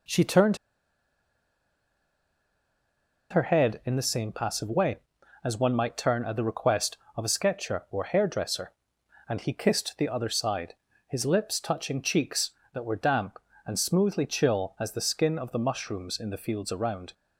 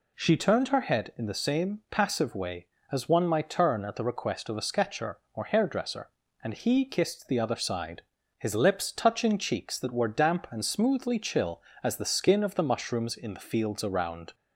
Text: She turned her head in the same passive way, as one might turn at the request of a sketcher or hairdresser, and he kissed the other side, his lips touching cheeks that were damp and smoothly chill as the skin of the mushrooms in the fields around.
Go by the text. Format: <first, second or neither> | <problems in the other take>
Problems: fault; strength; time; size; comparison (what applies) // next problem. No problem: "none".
second | pauses between "turned" and "her"; strong; at 0.5 s; 2.7 s long